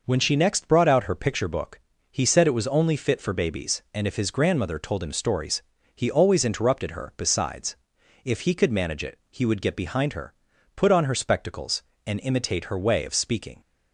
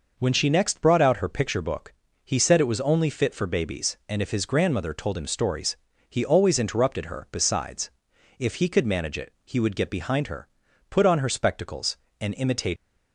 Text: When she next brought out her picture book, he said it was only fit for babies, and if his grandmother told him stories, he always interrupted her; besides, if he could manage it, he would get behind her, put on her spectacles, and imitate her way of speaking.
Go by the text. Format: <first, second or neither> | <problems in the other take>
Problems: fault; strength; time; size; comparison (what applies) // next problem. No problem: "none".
first | stops before "her way of speaking"; at 12.7 s